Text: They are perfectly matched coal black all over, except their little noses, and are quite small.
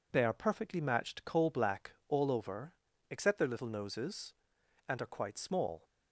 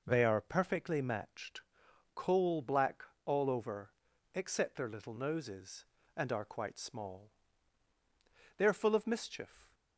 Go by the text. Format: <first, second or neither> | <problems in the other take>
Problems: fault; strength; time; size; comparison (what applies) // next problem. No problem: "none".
first | pauses between "matched" and "coal"; noticeable; at 1.6 s; 0.52 s long // pauses between "black" and "all"; slight; at 3.0 s; 0.20 s long; slight in the first // goes on to say "They are full of mischief"; noticeable; from 8.5 s on; 1.1 s long